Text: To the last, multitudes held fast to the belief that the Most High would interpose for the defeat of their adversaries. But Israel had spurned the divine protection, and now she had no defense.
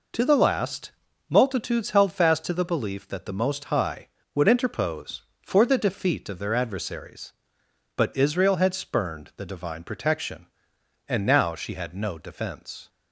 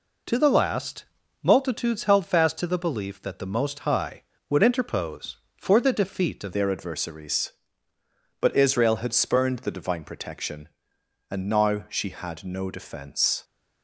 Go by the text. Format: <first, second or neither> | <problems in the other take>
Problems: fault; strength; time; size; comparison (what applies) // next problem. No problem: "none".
first | changes voice at "their"; from 6.5 s on; 6.9 s long